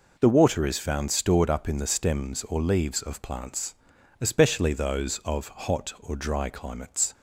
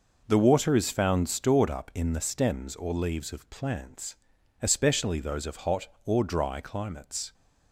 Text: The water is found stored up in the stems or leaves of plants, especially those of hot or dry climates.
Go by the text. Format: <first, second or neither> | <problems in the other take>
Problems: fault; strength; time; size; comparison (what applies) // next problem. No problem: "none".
neither | none